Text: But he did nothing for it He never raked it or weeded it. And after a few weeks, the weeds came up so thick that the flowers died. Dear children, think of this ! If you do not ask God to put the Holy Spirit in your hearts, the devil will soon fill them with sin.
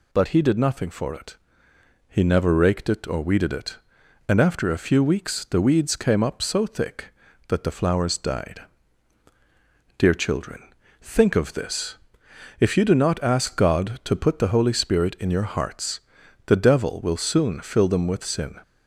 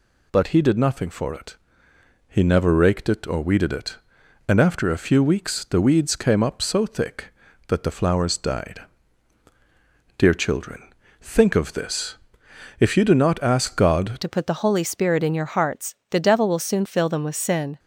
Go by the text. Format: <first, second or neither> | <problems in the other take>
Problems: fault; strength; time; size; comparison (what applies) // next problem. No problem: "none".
first | pauses between "it" and "He"; noticeable; at 1.5 s; 0.72 s long; noticeable in the first // changes voice at "to"; from 14.2 s on; 3.5 s long